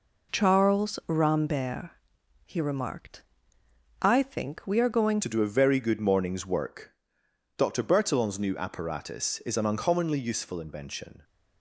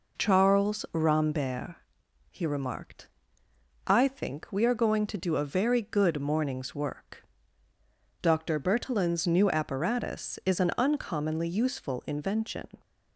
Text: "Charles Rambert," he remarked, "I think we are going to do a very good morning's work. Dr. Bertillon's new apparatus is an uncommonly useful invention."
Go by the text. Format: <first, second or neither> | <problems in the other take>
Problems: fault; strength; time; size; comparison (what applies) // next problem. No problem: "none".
second | changes voice at "to"; from 5.2 s on; 6.0 s long